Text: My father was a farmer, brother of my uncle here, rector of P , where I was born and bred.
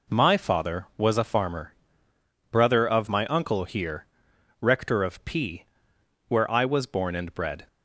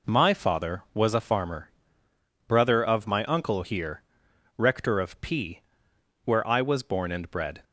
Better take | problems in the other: neither | none

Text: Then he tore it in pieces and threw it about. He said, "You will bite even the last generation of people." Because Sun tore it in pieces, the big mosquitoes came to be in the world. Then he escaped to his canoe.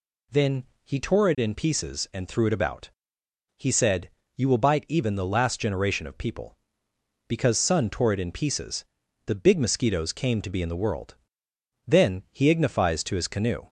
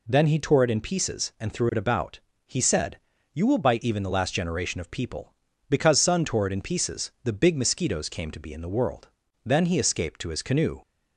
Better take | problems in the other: second | pauses between "Then" and "he"; slight; at 0.6 s; 0.20 s long // says "ignifies" for "escaped"; at 12.5 s

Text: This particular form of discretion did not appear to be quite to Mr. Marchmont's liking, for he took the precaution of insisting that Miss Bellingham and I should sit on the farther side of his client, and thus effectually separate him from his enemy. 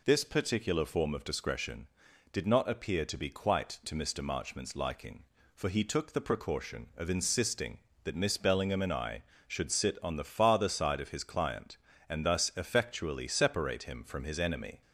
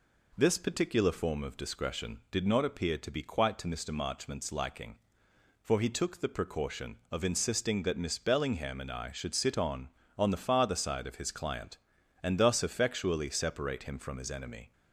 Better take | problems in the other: first | says "on" twice; at 10.1 s

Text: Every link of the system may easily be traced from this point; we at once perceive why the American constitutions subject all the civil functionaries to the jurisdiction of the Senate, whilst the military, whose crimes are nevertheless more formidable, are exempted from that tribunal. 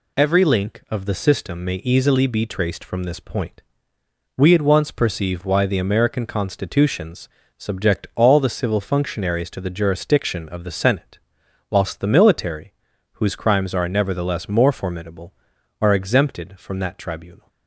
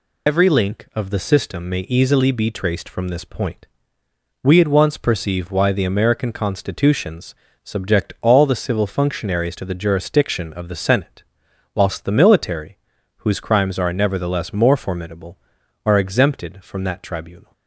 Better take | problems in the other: first | loses the start of "Every"; at 0.2 s; 60 ms // pauses between "constitutions" and "subject"; slight; at 7.3 s; 0.26 s long; slight in the first

